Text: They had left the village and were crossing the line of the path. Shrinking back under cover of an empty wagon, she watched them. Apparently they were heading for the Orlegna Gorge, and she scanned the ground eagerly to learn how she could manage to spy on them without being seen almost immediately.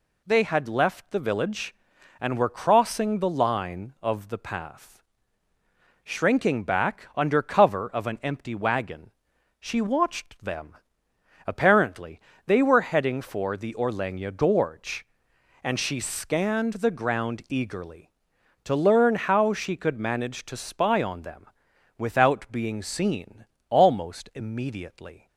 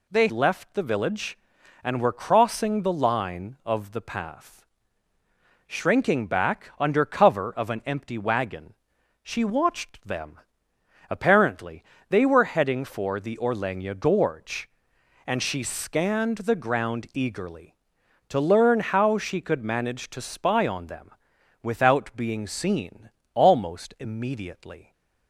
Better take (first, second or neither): first